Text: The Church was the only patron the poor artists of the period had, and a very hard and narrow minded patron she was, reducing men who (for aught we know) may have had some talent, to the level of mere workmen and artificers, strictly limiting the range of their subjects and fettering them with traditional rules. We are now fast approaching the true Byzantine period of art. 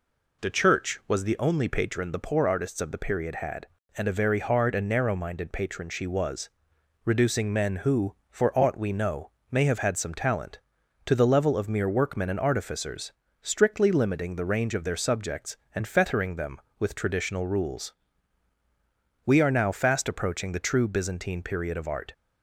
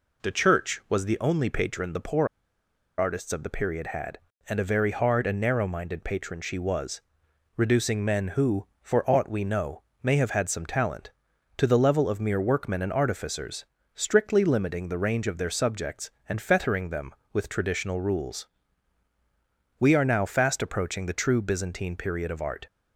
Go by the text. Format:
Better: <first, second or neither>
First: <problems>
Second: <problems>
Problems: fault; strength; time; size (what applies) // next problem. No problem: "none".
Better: first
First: none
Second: pauses between "poor" and "artists"; noticeable; at 2.2 s; 0.70 s long